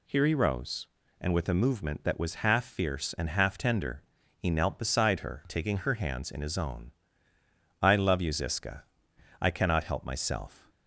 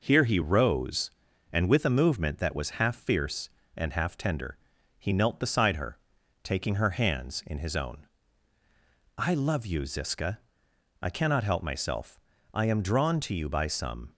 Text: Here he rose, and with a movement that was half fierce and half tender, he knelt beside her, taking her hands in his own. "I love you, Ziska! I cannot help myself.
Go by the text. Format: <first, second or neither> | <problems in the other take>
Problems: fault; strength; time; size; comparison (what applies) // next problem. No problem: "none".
first | goes on to say "I am drawn to you by some"; from 12.5 s on; 1.6 s long